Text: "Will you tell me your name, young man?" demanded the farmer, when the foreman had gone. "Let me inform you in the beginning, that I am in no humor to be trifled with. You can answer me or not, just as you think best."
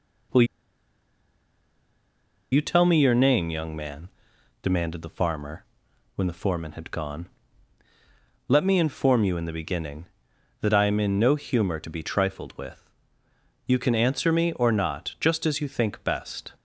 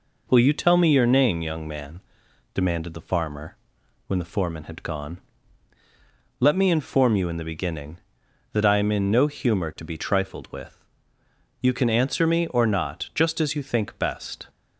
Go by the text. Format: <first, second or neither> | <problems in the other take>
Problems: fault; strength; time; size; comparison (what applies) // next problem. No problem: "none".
second | pauses between "Will" and "you"; strong; at 0.4 s; 2.0 s long